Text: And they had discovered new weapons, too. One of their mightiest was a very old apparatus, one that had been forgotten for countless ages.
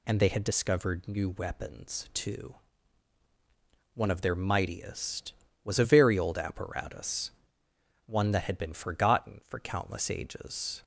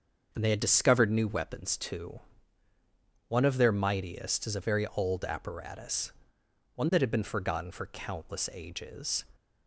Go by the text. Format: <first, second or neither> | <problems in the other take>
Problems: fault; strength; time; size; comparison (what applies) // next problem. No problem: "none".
first | starts louder than the rest; until 1.3 s; 6.5 dB // says "is" for "was"; at 4.4 s